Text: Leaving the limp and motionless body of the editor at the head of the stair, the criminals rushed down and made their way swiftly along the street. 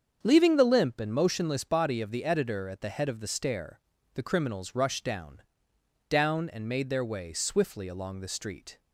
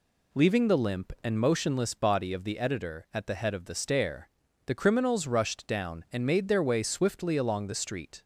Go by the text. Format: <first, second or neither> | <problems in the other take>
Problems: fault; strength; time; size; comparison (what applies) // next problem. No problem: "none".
second | starts louder than the rest; strong; until 1.2 s; 7 dB // says "down" twice; at 6.1 s